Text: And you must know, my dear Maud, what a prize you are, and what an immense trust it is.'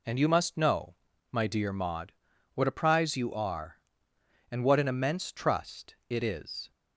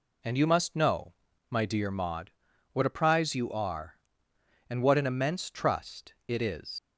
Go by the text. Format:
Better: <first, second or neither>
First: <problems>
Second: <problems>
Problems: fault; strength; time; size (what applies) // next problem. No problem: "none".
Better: first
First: none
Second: leaves "is" unfinished; at 6.7 s; 105 ms